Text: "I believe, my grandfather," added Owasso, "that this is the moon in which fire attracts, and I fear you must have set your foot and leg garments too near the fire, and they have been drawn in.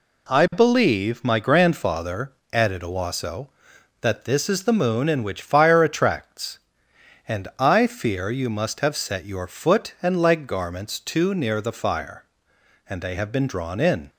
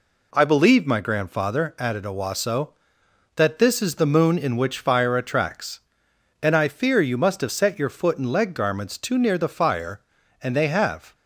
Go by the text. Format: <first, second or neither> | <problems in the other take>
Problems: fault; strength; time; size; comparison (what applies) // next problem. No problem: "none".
first | stops before "been drawn in"; at 11.1 s